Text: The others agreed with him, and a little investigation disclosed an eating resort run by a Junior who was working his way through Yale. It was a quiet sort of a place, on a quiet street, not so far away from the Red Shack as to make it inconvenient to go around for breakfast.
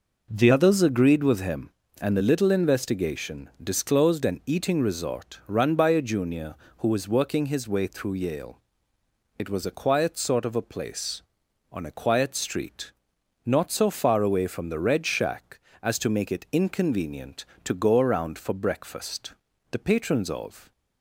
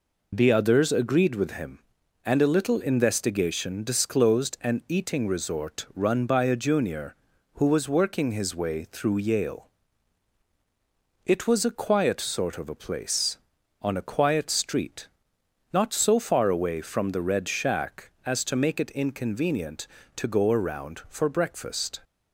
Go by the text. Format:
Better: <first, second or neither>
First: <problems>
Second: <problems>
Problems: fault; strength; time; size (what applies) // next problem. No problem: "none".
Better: second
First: goes on to say "The patrons of"; noticeable; from 19.6 s on; 1.0 s long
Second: none